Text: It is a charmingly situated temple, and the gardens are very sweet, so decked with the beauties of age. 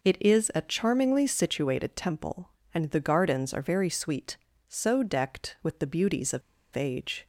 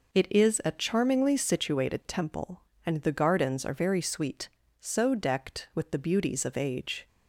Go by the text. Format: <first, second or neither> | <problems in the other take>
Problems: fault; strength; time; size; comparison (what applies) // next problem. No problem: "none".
second | pauses between "of" and "age"; slight; at 6.4 s; 0.33 s long